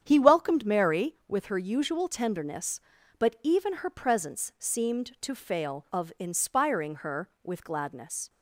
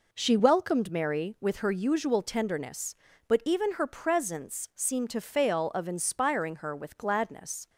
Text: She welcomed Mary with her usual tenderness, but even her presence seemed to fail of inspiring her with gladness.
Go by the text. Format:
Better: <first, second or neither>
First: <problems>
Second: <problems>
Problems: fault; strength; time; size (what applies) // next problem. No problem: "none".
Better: second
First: starts louder than the rest; strong; until 1.0 s; 8.5 dB // says "He" for "She"; at 0.0 s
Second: none